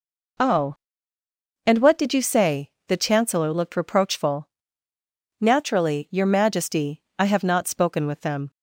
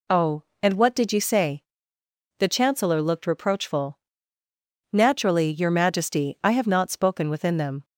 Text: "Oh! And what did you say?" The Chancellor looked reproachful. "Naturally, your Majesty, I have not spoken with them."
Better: first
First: none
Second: says "within" for "with"; at 7.3 s

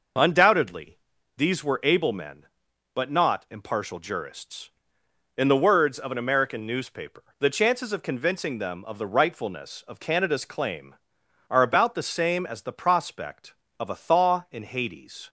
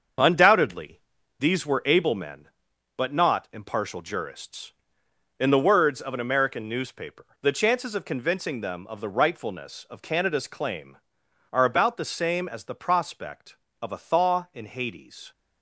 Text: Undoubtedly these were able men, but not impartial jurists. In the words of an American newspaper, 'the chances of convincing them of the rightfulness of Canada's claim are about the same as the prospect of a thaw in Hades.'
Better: first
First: pauses between "Undoubtedly" and "these"; at 0.9 s; 0.40 s long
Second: gets quieter; strong; throughout; 7 dB // pauses between "Undoubtedly" and "these"; at 0.9 s; 0.40 s long

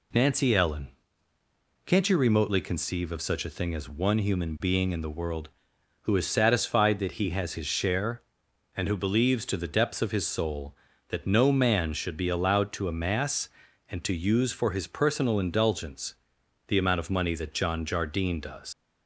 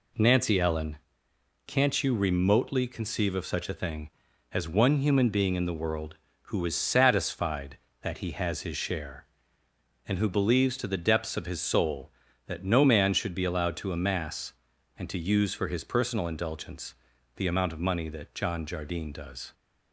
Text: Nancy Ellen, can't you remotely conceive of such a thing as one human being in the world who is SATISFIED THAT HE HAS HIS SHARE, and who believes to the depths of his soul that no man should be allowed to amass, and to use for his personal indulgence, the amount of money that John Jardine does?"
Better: second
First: leaves "does" unfinished; at 18.7 s; 110 ms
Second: none

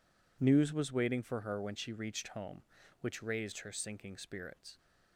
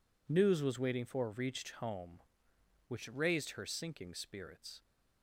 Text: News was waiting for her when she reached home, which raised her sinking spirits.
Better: first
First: none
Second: skips "her when she"; at 1.3 s

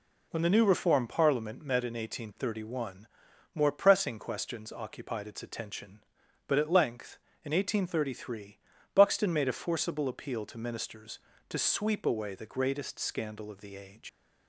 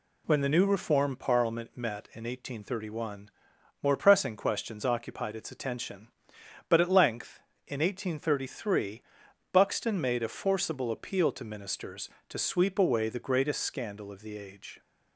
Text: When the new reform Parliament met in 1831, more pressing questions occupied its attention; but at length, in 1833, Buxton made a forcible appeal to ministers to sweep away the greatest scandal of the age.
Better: second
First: leaves "age" unfinished; at 14.0 s; 80 ms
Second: none

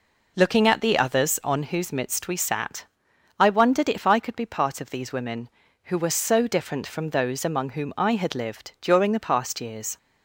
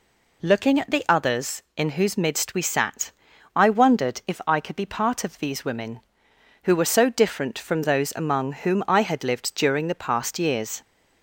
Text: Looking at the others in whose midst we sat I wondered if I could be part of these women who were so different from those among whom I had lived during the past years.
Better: second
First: says "on" for "in"; at 1.4 s // pauses between "sat" and "I"; noticeable; at 2.8 s; 0.52 s long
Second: pauses between "sat" and "I"; at 3.1 s; 0.44 s long

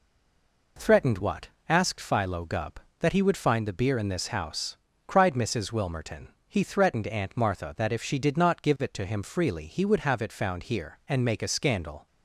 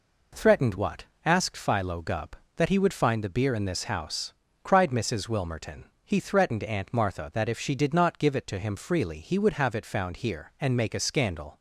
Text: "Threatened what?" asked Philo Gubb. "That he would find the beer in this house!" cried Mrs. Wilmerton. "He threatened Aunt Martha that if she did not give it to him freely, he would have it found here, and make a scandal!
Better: second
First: stays silent before the first word; slight; until 0.7 s; 0.7 s long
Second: none

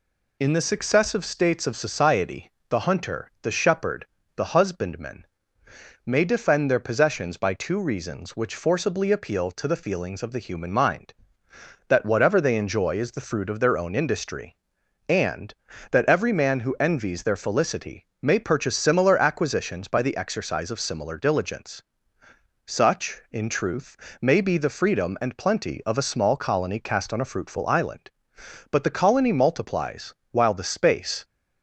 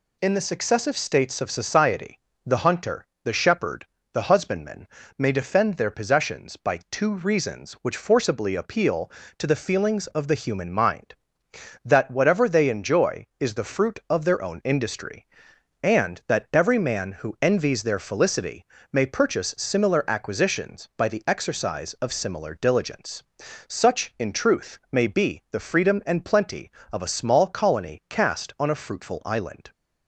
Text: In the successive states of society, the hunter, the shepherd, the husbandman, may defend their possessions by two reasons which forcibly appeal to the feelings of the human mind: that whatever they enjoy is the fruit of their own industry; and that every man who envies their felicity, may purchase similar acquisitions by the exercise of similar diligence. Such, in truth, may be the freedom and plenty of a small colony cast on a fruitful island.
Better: second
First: goes on to say "But the colony multiplies while the space"; strong; from 28.7 s on; 2.5 s long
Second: none

